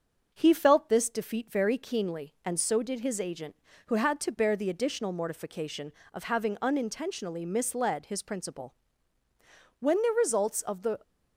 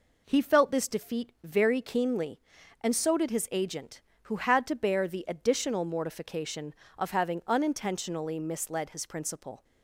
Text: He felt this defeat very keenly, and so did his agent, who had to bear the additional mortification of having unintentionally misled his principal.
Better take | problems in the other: second | starts louder than the rest; until 1.3 s; 6.5 dB // goes on to say "When the results of the"; noticeable; from 9.7 s on; 1.2 s long

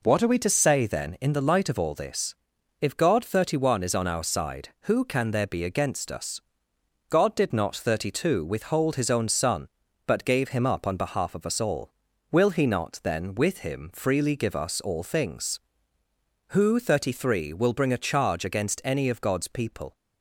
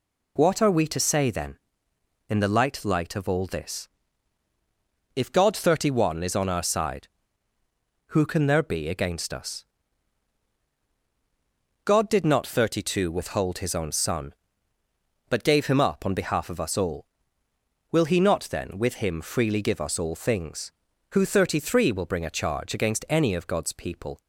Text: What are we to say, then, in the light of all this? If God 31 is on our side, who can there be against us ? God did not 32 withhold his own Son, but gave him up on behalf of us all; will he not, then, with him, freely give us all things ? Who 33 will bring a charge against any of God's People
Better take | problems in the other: first | says "light" twice; at 2.8 s

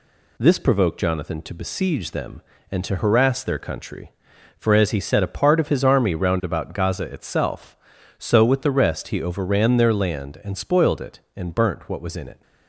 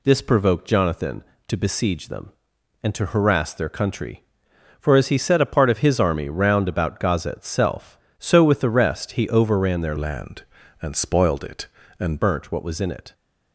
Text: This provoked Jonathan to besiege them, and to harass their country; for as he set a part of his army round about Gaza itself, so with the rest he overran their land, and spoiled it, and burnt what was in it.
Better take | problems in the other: first | changes voice from "land" to "and"; from 9.9 to 12.1 s; 2.2 s long

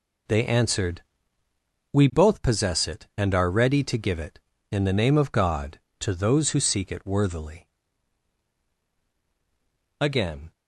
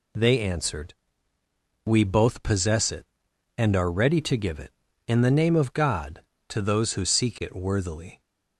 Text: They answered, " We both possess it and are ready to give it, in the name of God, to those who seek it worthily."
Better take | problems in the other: second | goes on to say "Again"; from 9.9 s on; 0.52 s long

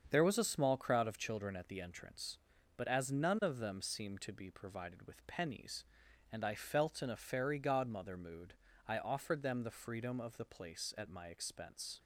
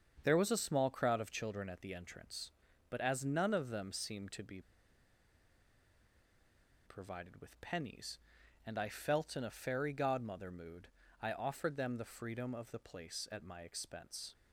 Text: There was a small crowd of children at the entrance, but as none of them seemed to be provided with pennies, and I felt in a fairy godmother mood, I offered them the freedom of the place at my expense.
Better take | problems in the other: first | starts louder than the rest; strong; until 1.2 s; 7 dB; strong in the first // pauses between "be" and "provided"; strong; at 4.6 s; 2.2 s long

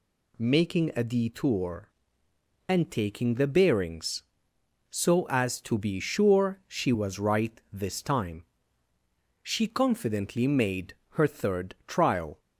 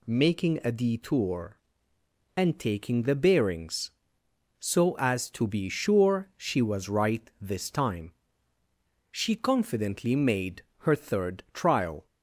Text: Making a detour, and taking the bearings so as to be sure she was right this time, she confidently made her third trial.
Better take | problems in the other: neither | pauses between "made" and "her"; slight; the same in both

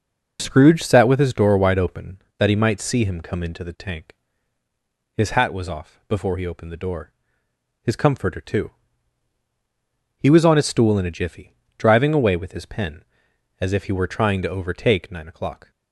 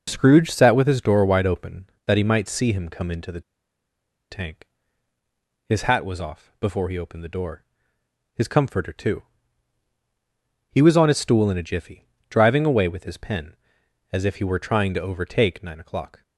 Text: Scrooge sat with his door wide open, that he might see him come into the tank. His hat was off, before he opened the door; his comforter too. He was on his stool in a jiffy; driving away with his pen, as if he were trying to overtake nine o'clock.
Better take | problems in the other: first | pauses between "the" and "tank"; noticeable; at 3.4 s; 0.90 s long

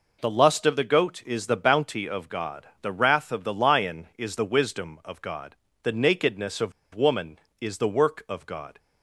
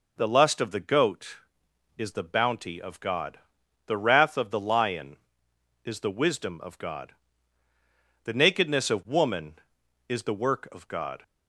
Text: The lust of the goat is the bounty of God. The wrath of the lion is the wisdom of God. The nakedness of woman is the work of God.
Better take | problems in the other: second | pauses between "of" and "woman"; slight; at 6.7 s; 0.22 s long

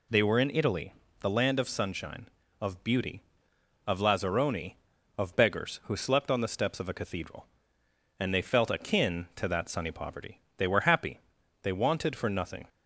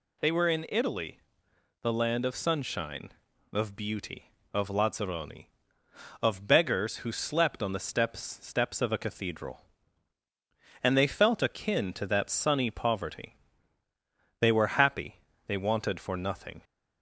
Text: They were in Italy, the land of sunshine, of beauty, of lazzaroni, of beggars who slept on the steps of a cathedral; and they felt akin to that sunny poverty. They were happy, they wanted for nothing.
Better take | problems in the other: first | says "steps" twice; at 8.4 s

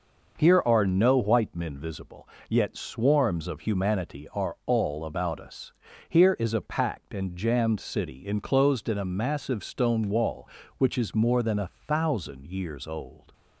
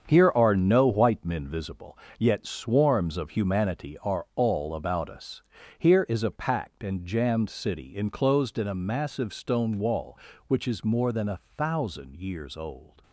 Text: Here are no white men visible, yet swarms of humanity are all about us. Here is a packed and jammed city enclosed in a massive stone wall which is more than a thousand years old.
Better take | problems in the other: first | gets quieter; strong; throughout; 8 dB // pauses between "a" and "thousand"; slight; at 11.4 s; 0.16 s long; slight in the first

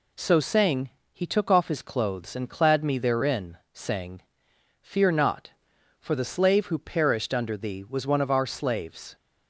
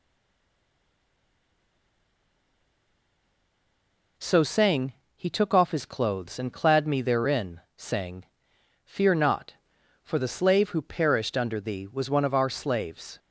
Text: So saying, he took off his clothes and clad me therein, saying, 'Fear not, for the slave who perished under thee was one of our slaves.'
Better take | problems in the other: first | stays silent before the first word; strong; until 4.1 s; 4.1 s long

